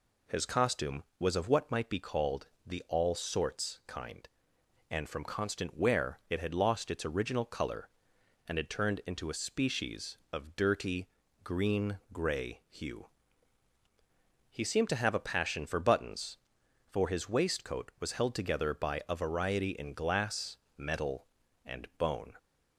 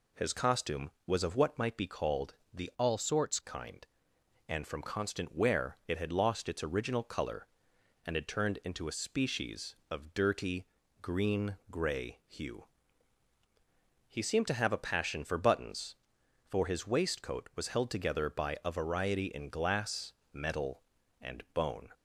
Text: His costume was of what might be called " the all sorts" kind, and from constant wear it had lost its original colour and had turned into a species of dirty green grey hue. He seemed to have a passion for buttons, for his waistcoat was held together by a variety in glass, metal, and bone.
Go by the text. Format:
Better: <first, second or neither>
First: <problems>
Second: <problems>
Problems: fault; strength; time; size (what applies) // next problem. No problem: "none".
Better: first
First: pauses between "dirty" and "green"; at 11.0 s; 0.38 s long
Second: changes voice from "all" to "sorts"; from 2.7 to 3.3 s; 0.6 s long // pauses between "dirty" and "green"; at 10.6 s; 0.38 s long